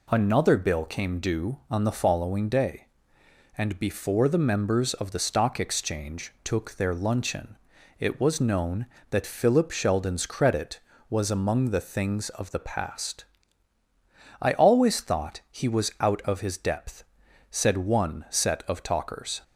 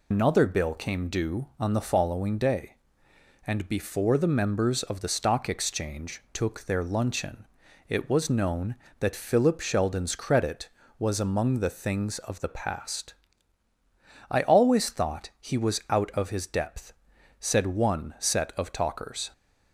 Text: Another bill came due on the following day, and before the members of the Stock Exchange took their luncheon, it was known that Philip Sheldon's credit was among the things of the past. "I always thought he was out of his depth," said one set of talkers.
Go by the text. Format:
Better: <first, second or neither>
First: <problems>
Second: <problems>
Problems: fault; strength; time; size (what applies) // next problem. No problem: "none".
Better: first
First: none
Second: loses the start of "Another"; at 0.1 s; 135 ms